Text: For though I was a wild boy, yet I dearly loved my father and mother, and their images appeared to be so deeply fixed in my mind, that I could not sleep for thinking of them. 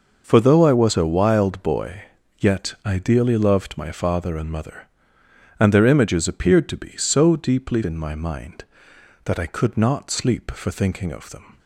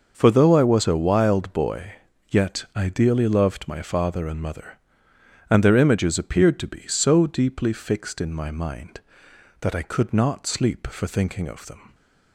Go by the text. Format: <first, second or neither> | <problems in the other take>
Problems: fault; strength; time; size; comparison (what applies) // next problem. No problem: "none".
second | skips "fixed"; at 7.8 s